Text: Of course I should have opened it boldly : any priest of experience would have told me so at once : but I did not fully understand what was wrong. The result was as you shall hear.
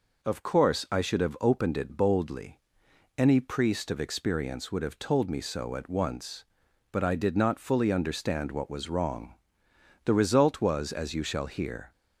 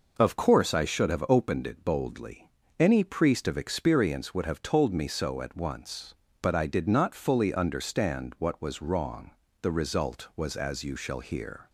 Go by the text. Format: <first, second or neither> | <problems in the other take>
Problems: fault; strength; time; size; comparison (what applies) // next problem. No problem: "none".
neither | none